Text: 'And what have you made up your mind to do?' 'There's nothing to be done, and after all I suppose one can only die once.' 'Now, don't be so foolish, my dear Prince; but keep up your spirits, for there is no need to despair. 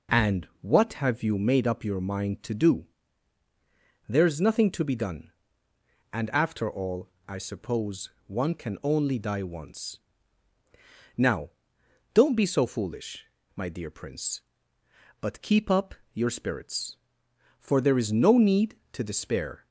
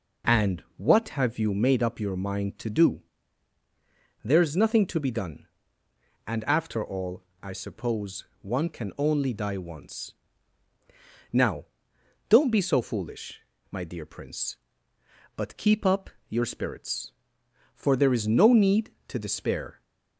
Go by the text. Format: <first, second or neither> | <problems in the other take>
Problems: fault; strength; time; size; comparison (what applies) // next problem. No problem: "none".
neither | pauses between "all" and "I"; slight; the same in both // pauses between "suppose" and "one"; slight; the same in both // pauses between "up" and "your"; slight; the same in both